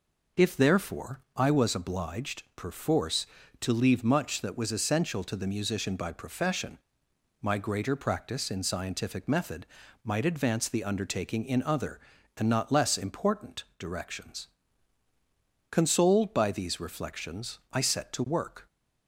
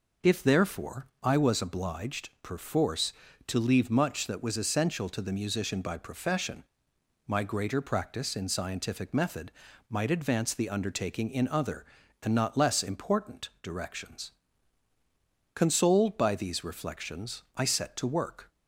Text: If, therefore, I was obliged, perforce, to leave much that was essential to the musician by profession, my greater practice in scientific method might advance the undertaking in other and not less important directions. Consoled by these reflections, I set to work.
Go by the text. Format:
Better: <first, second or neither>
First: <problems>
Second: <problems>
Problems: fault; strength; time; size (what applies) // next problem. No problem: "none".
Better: neither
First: pauses between "method" and "might"; at 9.6 s; 0.38 s long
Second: pauses between "method" and "might"; at 9.5 s; 0.38 s long